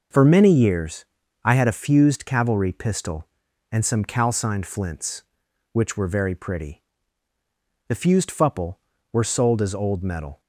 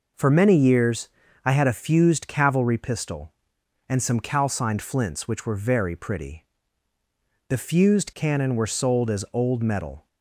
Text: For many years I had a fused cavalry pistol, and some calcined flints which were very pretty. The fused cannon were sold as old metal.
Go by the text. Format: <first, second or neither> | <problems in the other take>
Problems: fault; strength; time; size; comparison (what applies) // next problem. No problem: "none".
second | pauses between "years" and "I"; slight; at 1.0 s; 0.36 s long; slight in the second // says "fupple" for "cannon"; at 8.3 s